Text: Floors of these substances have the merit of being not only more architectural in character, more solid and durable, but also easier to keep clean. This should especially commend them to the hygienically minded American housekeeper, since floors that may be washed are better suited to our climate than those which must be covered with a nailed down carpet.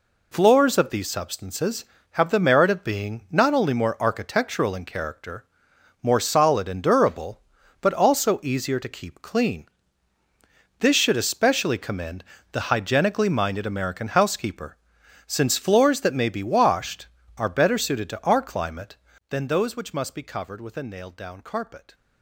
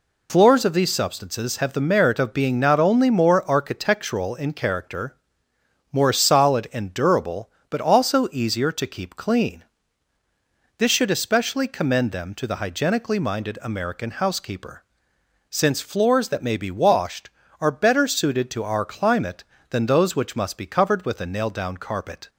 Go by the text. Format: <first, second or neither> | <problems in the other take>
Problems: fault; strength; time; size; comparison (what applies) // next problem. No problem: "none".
second | skips "them to"; at 12.3 s